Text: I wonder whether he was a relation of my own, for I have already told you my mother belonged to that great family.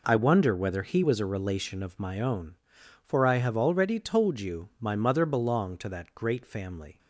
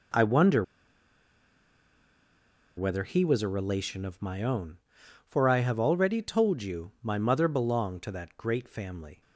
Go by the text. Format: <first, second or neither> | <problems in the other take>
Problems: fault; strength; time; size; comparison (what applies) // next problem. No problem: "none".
first | pauses between "wonder" and "whether"; strong; at 0.6 s; 2.1 s long